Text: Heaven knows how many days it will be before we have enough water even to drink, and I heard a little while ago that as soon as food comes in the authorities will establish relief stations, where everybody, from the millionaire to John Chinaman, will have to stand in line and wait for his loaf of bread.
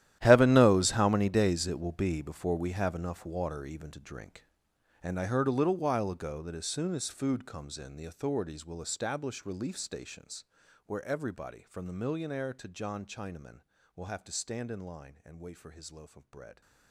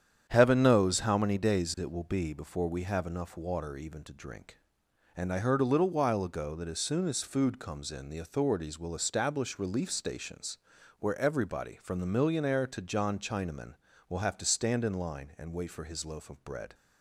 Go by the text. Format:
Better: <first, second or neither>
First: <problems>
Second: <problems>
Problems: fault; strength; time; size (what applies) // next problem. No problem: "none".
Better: second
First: gets quieter; strong; throughout; 17.5 dB // starts louder than the rest; strong; until 1.2 s; 12.5 dB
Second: starts louder than the rest; strong; until 1.3 s; 9 dB